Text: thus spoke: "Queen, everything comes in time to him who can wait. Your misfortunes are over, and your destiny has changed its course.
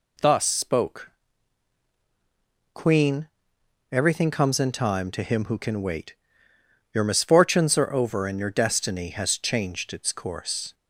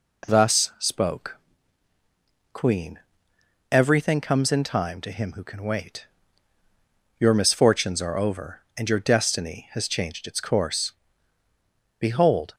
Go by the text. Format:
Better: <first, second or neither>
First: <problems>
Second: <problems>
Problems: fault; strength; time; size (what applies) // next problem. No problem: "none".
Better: first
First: none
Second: goes on to say "Behold"; from 11.9 s on; 0.56 s long